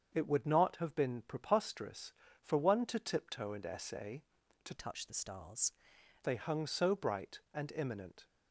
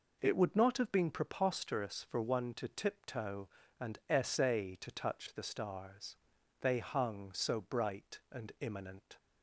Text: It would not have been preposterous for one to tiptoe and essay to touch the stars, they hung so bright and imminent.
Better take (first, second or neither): second